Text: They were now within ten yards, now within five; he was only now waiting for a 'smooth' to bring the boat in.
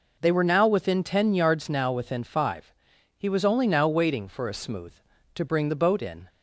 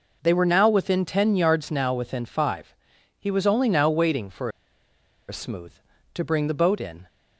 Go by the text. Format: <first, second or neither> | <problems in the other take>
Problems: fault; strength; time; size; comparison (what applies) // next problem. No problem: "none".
first | pauses between "for" and "a"; noticeable; at 4.4 s; 0.79 s long